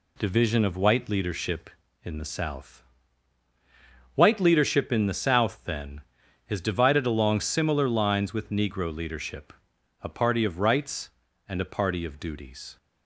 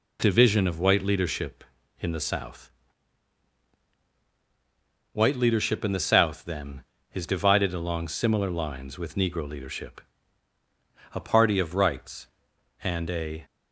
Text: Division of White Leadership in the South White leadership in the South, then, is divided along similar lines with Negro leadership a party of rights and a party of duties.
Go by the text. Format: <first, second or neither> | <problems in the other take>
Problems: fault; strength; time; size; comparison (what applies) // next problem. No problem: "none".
first | pauses between "South" and "White"; strong; at 2.6 s; 2.4 s long; strong in the first // pauses between "leadership" and "a"; at 9.9 s; 1.1 s long; noticeable in the first // stops before "party of duties"; at 13.4 s